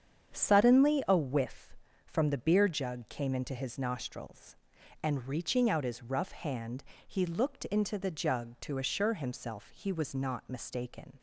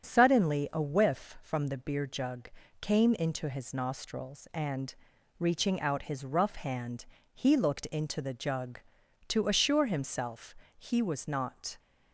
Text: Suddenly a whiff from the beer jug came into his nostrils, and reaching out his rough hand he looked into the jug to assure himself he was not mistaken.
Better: first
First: starts louder than the rest; strong; until 1.3 s; 8 dB // pauses between "hand" and "he"; slight; at 6.8 s; 0.24 s long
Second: starts louder than the rest; strong; until 1.0 s; 7.5 dB // pauses between "jug" and "came"; slight; at 2.5 s; 0.32 s long // pauses between "and" and "reaching"; at 4.9 s; 0.44 s long // pauses between "hand" and "he"; slight; at 7.0 s; 0.26 s long // pauses between "himself" and "he"; slight; at 10.5 s; 0.22 s long // stops before "mistaken"; at 11.7 s

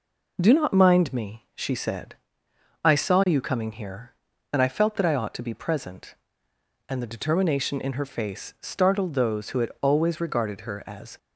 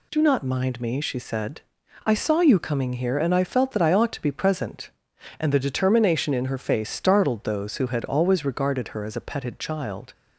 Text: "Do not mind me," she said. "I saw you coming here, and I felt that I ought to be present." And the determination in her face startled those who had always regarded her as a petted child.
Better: second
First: stops before "a petted child"; at 11.1 s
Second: none

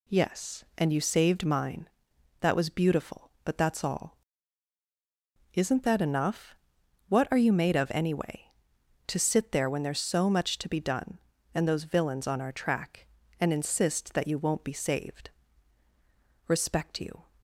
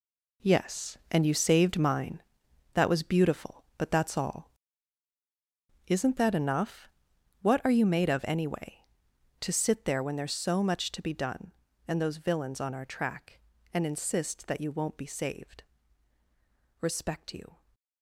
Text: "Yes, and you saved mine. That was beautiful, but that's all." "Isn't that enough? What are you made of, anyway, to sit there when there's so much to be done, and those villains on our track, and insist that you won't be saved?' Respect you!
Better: first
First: none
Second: gets quieter; strong; throughout; 10.5 dB

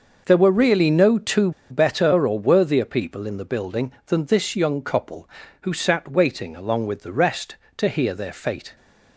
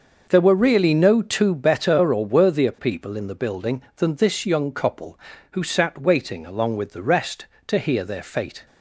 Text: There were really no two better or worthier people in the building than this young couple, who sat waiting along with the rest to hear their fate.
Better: second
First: pauses between "two" and "better"; slight; at 1.5 s; 0.20 s long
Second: none

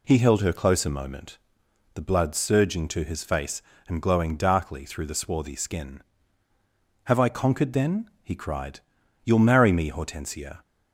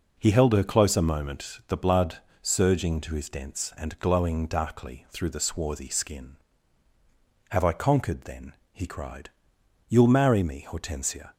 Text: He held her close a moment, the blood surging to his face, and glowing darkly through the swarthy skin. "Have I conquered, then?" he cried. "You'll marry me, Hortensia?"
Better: first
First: none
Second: pauses between "blood" and "surging"; slight; at 2.1 s; 0.24 s long // says "dents" for "face"; at 3.2 s

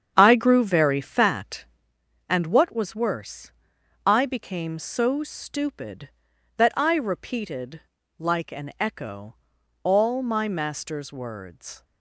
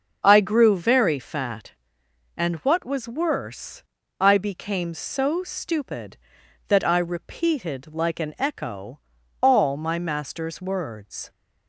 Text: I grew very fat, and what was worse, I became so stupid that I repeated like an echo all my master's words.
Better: second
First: starts louder than the rest; strong; until 1.9 s; 8 dB // pauses between "repeated" and "like"; at 7.7 s; 0.38 s long // pauses between "echo" and "all"; noticeable; at 9.3 s; 0.46 s long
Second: pauses between "echo" and "all"; at 8.9 s; 0.42 s long

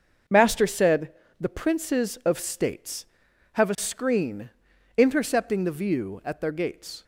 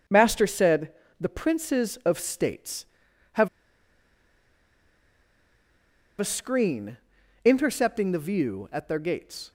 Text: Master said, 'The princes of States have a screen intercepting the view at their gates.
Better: first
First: starts louder than the rest; until 1.5 s; 6.5 dB // pauses between "screen" and "intercepting"; noticeable; at 4.4 s; 0.48 s long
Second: starts louder than the rest; until 1.3 s; 6.5 dB // pauses between "have" and "a"; strong; at 3.4 s; 2.7 s long // pauses between "screen" and "intercepting"; noticeable; at 6.9 s; 0.48 s long

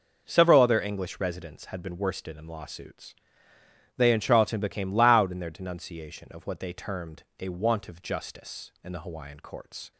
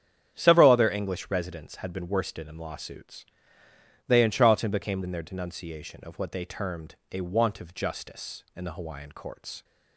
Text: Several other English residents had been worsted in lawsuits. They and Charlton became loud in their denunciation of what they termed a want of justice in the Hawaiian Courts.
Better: first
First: pauses between "termed" and "a"; slight; at 7.2 s; 0.16 s long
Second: starts louder than the rest; strong; until 1.3 s; 9 dB // skips "loud"; at 5.0 s // pauses between "termed" and "a"; slight; at 6.9 s; 0.16 s long

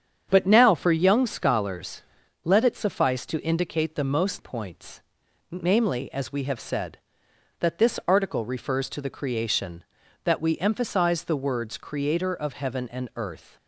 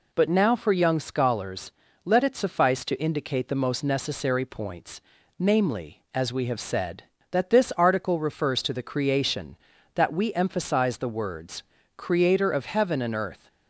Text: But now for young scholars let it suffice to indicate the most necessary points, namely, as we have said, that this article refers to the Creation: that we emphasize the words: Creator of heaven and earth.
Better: second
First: starts louder than the rest; strong; until 1.3 s; 8 dB // pauses between "scholars" and "let"; at 2.0 s; 0.40 s long // skips "necessary"; at 4.3 s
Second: pauses between "scholars" and "let"; slight; at 1.7 s; 0.32 s long

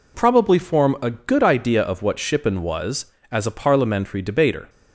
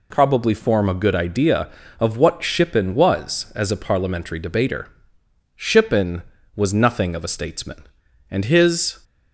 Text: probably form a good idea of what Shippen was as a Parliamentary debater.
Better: first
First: none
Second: goes on to say "Shippen was nothing of a statesman and his"; strong; from 5.5 s on; 3.4 s long

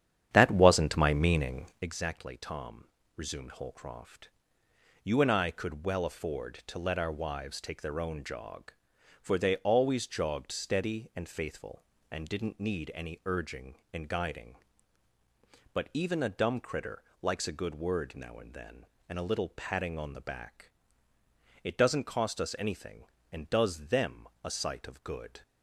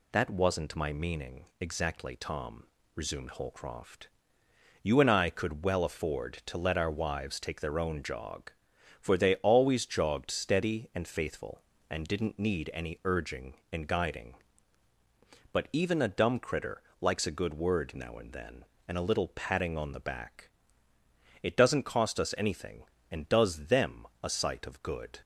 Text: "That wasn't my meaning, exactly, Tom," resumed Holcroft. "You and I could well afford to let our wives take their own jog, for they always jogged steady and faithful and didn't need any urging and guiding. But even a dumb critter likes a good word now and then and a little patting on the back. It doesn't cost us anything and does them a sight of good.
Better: second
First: starts louder than the rest; strong; until 1.9 s; 9.5 dB // pauses between "critter" and "likes"; slight; at 17.0 s; 0.18 s long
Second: pauses between "critter" and "likes"; slight; at 16.8 s; 0.18 s long

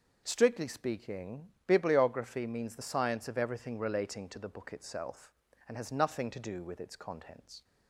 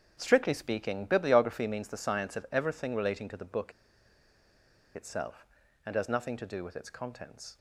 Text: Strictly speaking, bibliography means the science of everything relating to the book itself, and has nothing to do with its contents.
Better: first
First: starts louder than the rest; noticeable; until 1.2 s; 6 dB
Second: starts louder than the rest; strong; until 1.2 s; 8.5 dB // pauses between "book" and "itself"; at 3.7 s; 1.2 s long

